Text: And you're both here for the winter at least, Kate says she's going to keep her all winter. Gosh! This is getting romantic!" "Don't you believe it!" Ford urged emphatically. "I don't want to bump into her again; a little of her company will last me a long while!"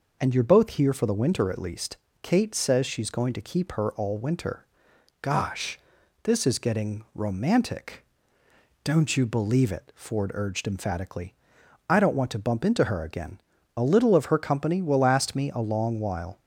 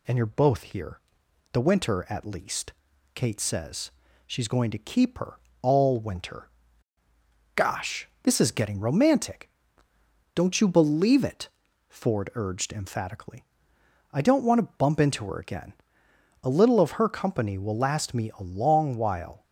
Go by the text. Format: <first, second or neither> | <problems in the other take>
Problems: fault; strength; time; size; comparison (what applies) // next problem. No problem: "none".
first | skips "for"; at 1.2 s // pauses between "says" and "she's"; slight; at 3.8 s; 0.36 s long // pauses between "her" and "all"; slight; at 5.3 s; 0.26 s long